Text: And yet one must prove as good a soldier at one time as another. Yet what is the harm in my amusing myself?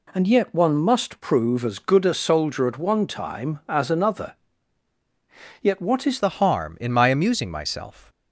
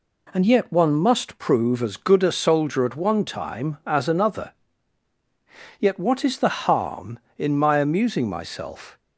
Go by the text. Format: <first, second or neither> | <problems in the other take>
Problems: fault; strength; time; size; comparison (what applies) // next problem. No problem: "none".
second | changes voice at "the"; from 6.1 s on; 1.9 s long